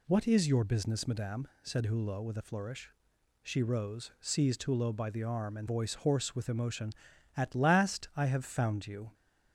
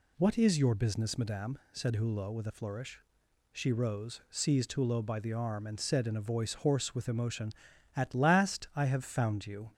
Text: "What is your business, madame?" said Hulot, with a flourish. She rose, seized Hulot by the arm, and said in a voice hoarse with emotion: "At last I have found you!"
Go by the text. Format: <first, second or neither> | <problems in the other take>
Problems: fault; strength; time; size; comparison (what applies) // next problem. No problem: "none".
second | skips "said in a"; at 5.6 s